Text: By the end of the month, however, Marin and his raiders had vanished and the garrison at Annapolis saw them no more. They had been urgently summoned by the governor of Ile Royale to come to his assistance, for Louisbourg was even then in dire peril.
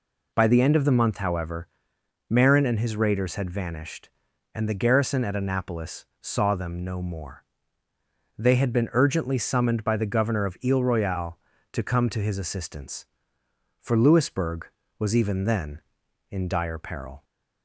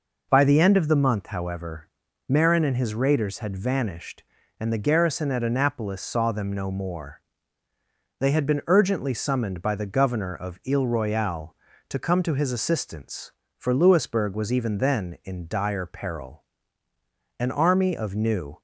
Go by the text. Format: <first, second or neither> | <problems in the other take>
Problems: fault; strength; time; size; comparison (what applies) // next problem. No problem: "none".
first | goes on to say "An army of New"; noticeable; from 17.3 s on; 1.2 s long